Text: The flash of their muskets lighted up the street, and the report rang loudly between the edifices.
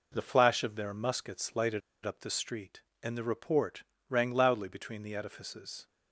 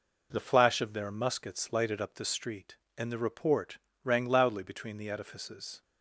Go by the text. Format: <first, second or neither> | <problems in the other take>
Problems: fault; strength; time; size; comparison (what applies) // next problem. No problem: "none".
second | pauses between "lighted" and "up"; slight; at 1.8 s; 0.24 s long // pauses between "report" and "rang"; slight; at 3.8 s; 0.26 s long; slight in the second